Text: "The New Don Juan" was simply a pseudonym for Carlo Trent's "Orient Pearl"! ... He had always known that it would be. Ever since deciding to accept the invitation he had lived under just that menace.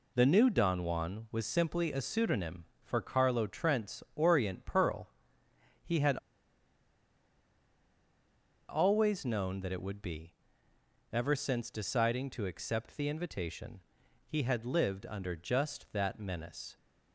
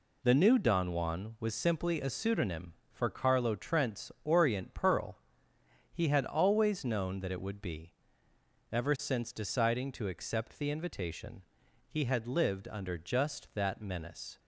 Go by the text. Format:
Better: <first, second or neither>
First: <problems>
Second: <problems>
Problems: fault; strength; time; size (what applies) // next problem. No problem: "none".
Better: second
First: pauses between "had" and "always"; strong; at 6.1 s; 2.5 s long // pauses between "invitation" and "he"; noticeable; at 13.8 s; 0.46 s long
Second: pauses between "invitation" and "he"; noticeable; at 11.4 s; 0.46 s long